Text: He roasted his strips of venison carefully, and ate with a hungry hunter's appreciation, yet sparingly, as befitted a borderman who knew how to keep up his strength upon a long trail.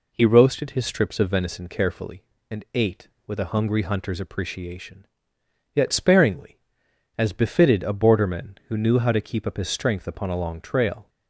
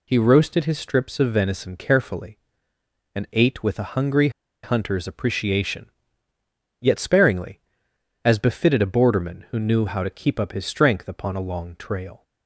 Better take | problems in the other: first | pauses between "hungry" and "hunter's"; slight; at 4.2 s; 0.33 s long

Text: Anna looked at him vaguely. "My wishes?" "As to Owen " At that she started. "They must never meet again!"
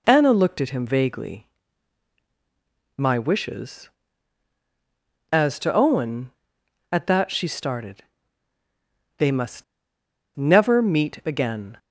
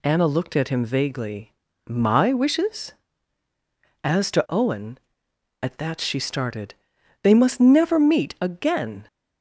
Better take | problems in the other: second | pauses between "must" and "never"; noticeable; at 9.6 s; 0.71 s long

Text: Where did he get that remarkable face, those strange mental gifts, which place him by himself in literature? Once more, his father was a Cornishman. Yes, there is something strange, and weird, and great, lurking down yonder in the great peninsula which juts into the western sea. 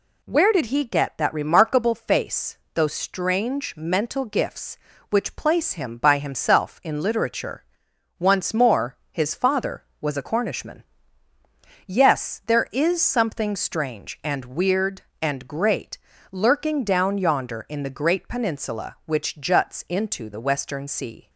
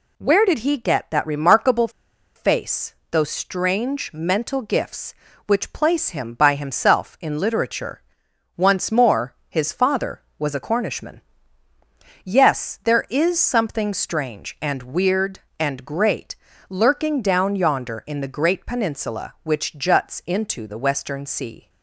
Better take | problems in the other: first | pauses between "remarkable" and "face"; noticeable; at 1.8 s; 0.46 s long

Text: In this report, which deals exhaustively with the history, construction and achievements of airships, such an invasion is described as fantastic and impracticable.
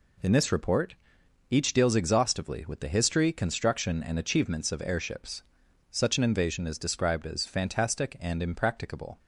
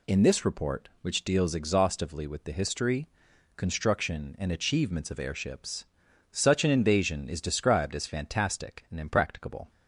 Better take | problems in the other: second | says "each" for "which"; at 1.5 s

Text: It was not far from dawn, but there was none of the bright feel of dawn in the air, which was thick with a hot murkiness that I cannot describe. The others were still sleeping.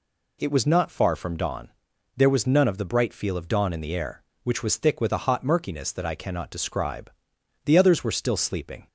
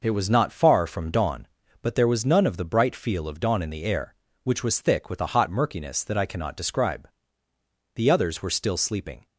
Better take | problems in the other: second | skips "but"; at 1.9 s

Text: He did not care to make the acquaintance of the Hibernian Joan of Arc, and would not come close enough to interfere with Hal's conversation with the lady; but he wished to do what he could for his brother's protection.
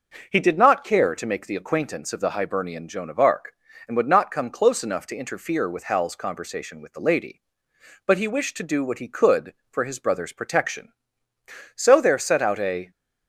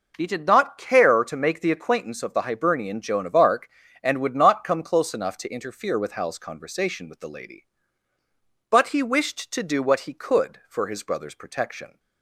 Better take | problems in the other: second | goes on to say "So there set out a"; noticeable; from 11.7 s on; 1.1 s long

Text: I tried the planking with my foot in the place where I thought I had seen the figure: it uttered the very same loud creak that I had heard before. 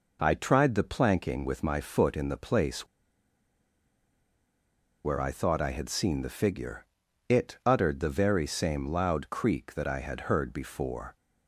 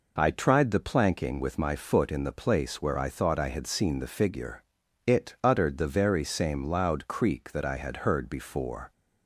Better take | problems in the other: second | pauses between "place" and "where"; strong; at 2.8 s; 2.1 s long

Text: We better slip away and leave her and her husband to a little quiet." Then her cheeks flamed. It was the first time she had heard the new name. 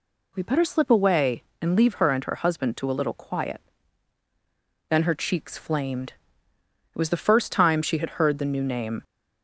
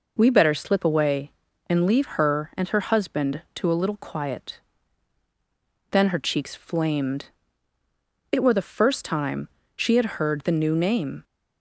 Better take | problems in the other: first | says "were" for "was"; at 8.4 s // pauses between "time" and "she"; slight; at 9.4 s; 0.28 s long

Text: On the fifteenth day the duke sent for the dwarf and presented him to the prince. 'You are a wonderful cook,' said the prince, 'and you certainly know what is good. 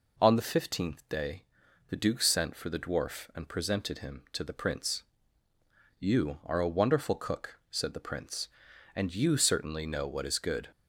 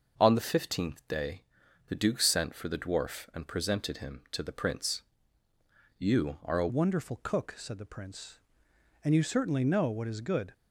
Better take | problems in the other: first | starts louder than the rest; noticeable; until 1.2 s; 6 dB // pauses between "day" and "the"; noticeable; at 1.4 s; 0.48 s long; noticeable in the first // changes voice at "wonderful"; from 6.6 s on; 3.9 s long

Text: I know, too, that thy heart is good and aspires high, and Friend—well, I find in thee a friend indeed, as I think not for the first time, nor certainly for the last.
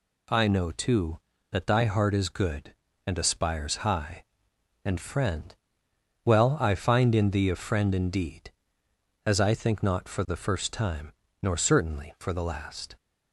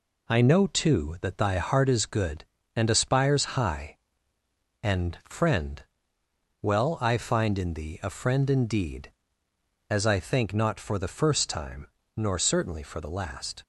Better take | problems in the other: neither | none

